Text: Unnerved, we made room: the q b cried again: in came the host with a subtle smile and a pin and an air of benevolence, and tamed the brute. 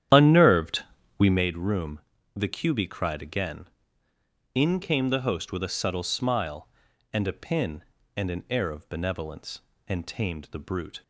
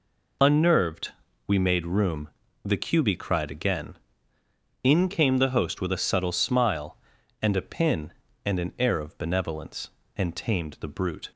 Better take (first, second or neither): second